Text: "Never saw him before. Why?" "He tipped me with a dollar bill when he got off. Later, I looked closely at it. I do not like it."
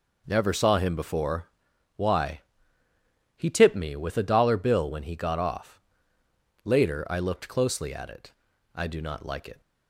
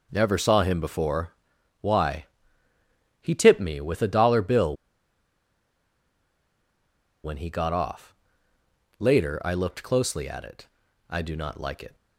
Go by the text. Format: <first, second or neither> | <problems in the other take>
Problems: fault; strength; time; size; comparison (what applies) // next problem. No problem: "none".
first | pauses between "bill" and "when"; strong; at 4.7 s; 2.4 s long